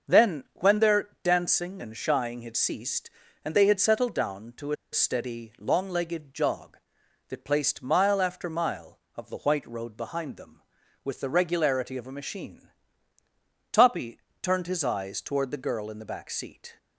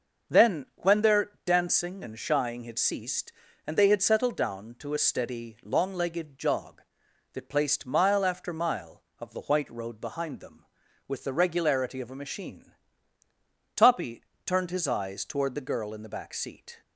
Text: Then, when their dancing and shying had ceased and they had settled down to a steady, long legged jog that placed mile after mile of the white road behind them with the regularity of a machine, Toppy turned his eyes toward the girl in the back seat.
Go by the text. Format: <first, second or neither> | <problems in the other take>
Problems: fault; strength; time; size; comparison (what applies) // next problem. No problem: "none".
second | starts louder than the rest; noticeable; until 1.3 s; 6 dB; noticeable in the second // pauses between "a" and "steady"; slight; at 4.7 s; 0.17 s long // pauses between "Toppy" and "turned"; slight; at 14.1 s; 0.22 s long; slight in the second